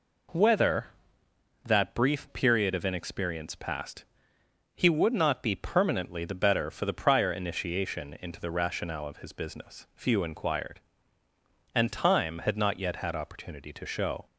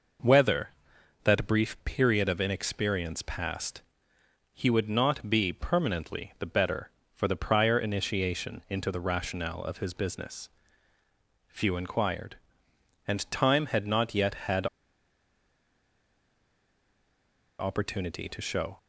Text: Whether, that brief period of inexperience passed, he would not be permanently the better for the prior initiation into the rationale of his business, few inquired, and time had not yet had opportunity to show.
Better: first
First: none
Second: pauses between "had" and "opportunity"; strong; at 14.6 s; 2.9 s long

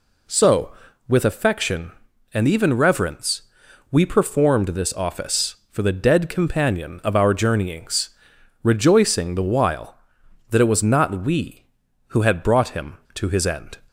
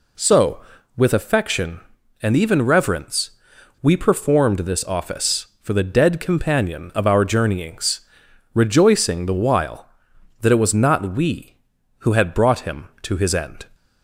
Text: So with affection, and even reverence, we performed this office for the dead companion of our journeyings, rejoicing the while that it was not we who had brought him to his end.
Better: neither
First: none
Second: none

